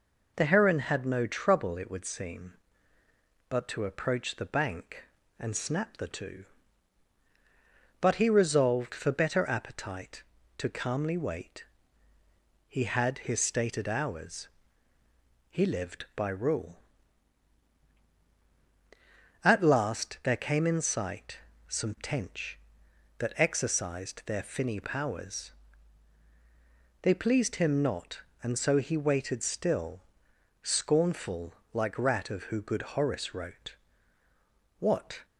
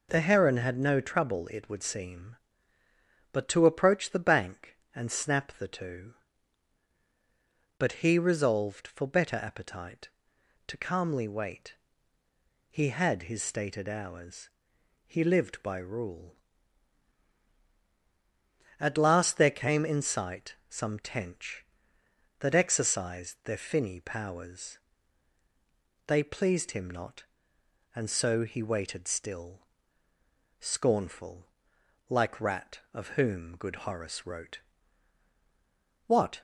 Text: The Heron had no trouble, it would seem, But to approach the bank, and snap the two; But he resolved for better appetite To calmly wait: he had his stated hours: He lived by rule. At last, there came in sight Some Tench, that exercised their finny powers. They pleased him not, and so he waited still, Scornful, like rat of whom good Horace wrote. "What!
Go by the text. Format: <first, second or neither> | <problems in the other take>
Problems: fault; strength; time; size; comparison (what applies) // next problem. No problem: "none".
second | pauses between "sight" and "Some"; slight; at 21.4 s; 0.28 s long // says "who" for "whom"; at 32.4 s